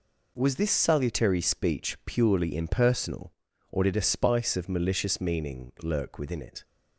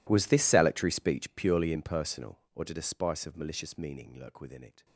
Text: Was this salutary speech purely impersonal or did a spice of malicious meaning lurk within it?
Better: first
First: none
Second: gets quieter; strong; throughout; 23 dB

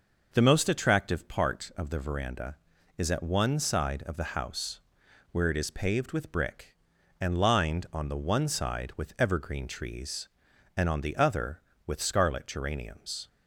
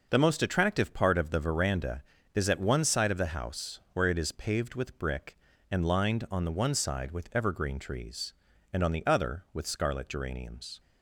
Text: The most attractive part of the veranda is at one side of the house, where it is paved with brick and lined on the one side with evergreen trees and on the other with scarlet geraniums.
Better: neither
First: none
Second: none

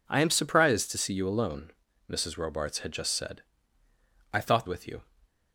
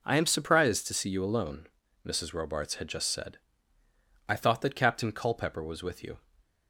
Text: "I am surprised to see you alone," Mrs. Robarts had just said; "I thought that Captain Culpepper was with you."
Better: second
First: skips "that Captain Culpepper was"; at 4.6 s // stays silent after the last word; slight; from 5.0 s on; 0.5 s long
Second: stays silent after the last word; slight; from 6.1 s on; 0.5 s long

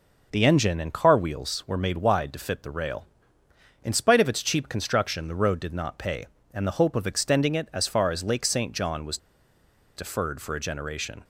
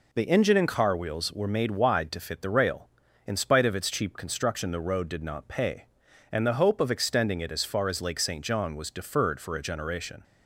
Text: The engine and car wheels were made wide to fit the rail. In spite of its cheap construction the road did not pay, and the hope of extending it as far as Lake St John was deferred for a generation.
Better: second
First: pauses between "was" and "deferred"; noticeable; at 9.1 s; 0.79 s long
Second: none

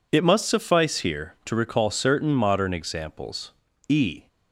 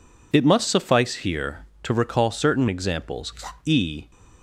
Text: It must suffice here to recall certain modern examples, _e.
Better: first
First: none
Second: skips "modern"; at 2.6 s

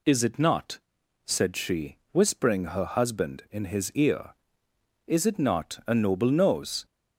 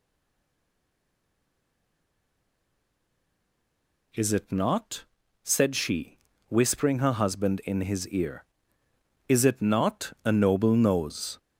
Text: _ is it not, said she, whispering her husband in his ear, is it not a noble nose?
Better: first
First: none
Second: stays silent before the first word; strong; until 4.1 s; 4.1 s long

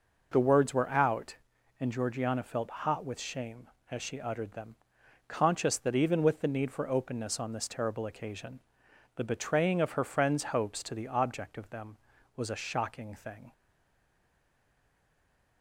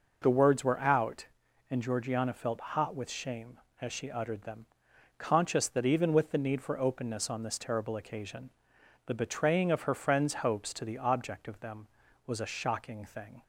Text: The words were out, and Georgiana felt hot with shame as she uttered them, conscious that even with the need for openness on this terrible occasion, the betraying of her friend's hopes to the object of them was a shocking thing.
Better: second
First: stays silent after the last word; noticeable; from 13.5 s on; 2.1 s long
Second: none

